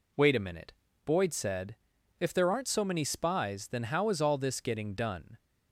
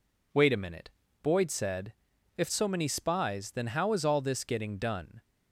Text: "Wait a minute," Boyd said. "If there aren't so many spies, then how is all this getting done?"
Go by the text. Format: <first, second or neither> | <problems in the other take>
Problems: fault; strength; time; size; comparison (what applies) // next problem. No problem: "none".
first | skips "there aren't"; at 2.4 s